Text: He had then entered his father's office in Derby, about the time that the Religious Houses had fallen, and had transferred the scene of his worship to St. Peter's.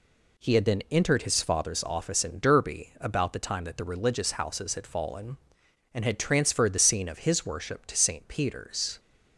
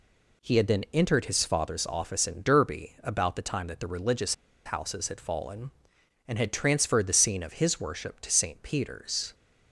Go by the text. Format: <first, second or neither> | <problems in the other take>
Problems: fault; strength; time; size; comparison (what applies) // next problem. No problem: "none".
first | pauses between "Religious" and "Houses"; slight; at 4.3 s; 0.30 s long